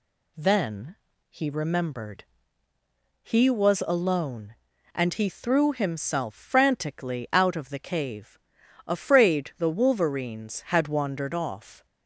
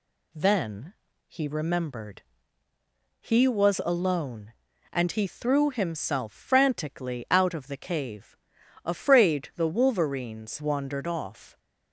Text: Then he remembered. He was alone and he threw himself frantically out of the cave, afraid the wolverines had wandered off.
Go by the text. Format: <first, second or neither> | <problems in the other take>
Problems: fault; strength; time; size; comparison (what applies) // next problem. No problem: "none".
first | pauses between "Then" and "he"; slight; at 0.9 s; 0.34 s long; slight in the first // skips "had"; at 10.6 s